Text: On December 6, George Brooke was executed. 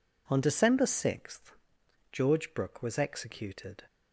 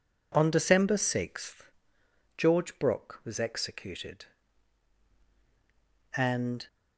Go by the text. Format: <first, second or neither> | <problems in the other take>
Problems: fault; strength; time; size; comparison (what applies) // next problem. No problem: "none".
first | goes on to say "And"; from 6.1 s on; 0.50 s long